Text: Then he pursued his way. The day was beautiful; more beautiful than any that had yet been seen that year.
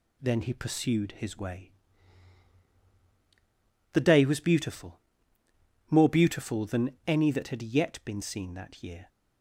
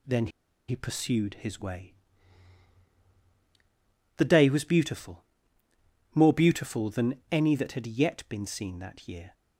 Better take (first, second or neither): first